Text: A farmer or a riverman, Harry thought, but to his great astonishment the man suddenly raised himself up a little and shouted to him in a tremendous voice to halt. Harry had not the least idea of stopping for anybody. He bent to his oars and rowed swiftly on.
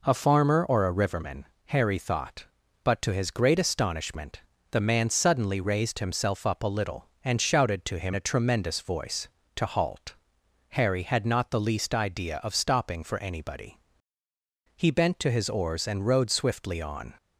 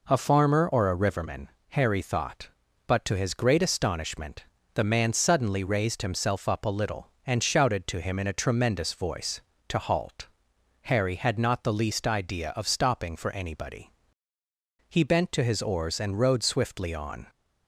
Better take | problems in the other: second | pauses between "astonishment" and "the"; slight; at 4.3 s; 0.32 s long; slight in the second // skips "in"; at 8.1 s

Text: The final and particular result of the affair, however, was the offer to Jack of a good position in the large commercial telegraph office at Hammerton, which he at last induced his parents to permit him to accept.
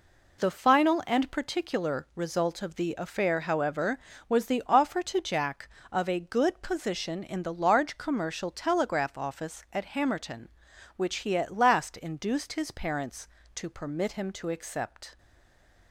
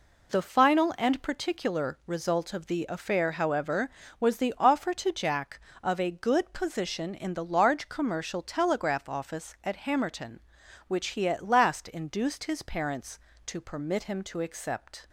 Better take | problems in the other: second | stays silent after the last word; slight; from 15.1 s on; 0.8 s long

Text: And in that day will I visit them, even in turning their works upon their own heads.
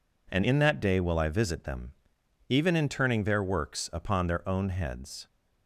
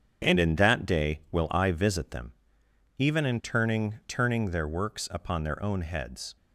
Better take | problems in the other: first | starts louder than the rest; strong; until 1.3 s; 7.5 dB // says "turning" twice; at 4.0 s

